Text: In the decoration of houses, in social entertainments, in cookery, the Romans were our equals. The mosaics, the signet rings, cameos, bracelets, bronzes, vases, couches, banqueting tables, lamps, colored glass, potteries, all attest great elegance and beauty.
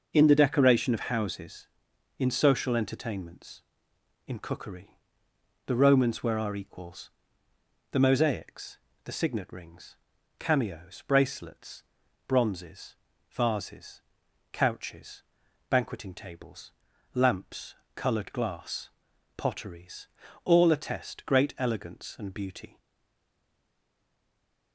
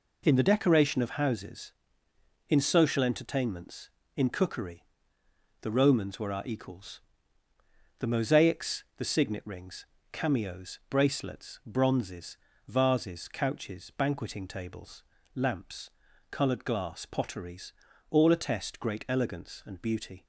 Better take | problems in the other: second | stays silent after the last word; noticeable; from 22.7 s on; 2.0 s long

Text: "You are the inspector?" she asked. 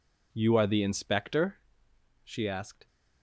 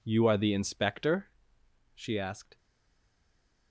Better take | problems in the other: first | stays silent after the last word; from 2.5 s on; 1.2 s long

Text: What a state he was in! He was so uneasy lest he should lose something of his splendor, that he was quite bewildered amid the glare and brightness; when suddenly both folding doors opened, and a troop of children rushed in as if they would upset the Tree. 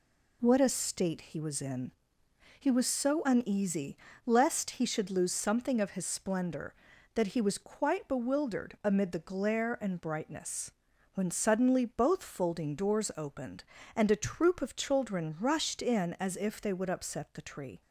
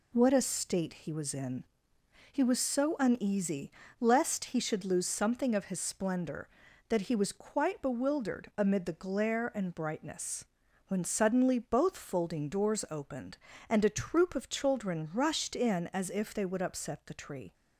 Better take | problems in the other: neither | pauses between "uneasy" and "lest"; slight; the same in both

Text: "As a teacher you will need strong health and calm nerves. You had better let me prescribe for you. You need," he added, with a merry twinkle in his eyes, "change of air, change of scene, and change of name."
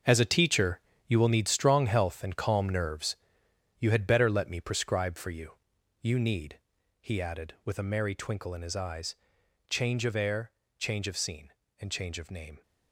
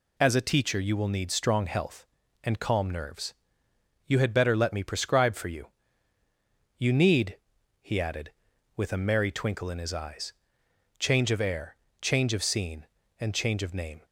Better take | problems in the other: second | gets quieter; strong; throughout; 10.5 dB // pauses between "teacher" and "you"; slight; at 0.7 s; 0.28 s long

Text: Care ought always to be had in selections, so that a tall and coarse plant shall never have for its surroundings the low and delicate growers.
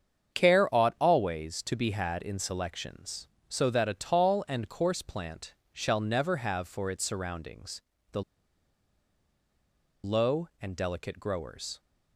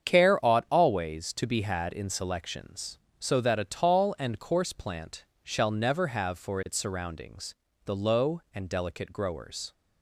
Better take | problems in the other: second | starts louder than the rest; strong; until 1.4 s; 7.5 dB; strong in the second // pauses between "plant" and "shall"; slight; at 5.5 s; 0.20 s long; slight in the second // pauses between "surroundings" and "the"; slight; at 7.8 s; 0.30 s long; slight in the second // pauses between "the" and "low"; strong; at 8.2 s; 1.8 s long

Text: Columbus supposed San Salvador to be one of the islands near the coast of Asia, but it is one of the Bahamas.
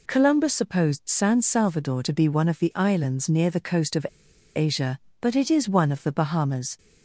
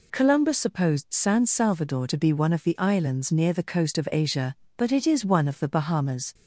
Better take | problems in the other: second | pauses between "of" and "Asia"; noticeable; at 4.0 s; 0.49 s long

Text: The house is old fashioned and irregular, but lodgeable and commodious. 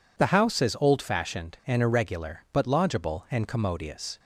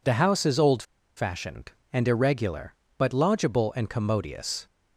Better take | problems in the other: first | pauses between "old" and "fashioned"; slight; at 0.8 s; 0.34 s long

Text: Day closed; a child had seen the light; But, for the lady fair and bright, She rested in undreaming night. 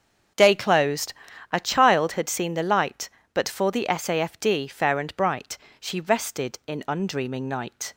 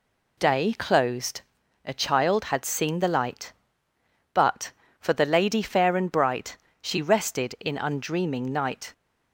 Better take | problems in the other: second | starts louder than the rest; until 1.7 s; 7 dB // says "safd" for "lady"; at 3.8 s

